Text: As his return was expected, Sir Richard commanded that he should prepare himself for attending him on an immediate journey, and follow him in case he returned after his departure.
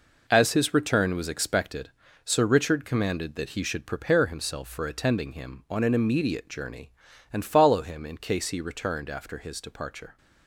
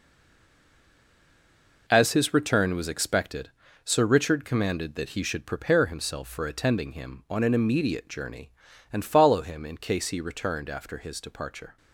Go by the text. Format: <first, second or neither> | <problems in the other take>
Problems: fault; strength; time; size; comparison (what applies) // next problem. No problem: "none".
first | stays silent before the first word; noticeable; until 1.8 s; 1.8 s long